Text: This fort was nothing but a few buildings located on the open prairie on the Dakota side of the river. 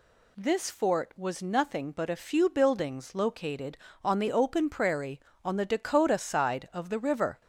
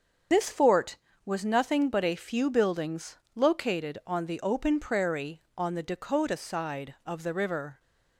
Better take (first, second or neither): first